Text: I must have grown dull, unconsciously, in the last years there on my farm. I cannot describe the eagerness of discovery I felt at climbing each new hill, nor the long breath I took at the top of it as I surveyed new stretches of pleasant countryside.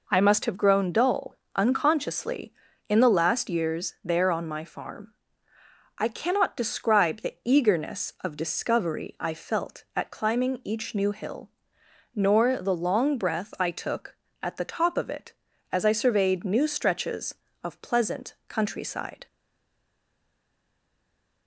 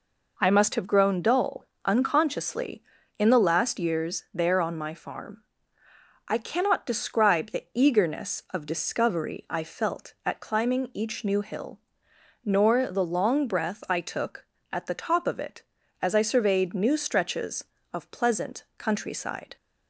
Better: second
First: stays silent after the last word; from 19.2 s on; 2.2 s long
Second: none

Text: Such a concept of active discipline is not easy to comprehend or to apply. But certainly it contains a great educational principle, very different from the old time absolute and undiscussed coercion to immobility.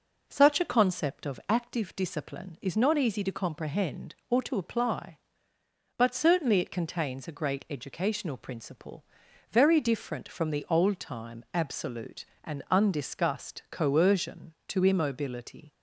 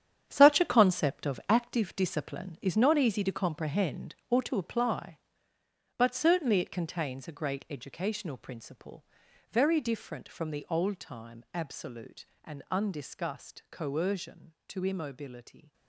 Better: first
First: none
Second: gets quieter; strong; throughout; 11 dB

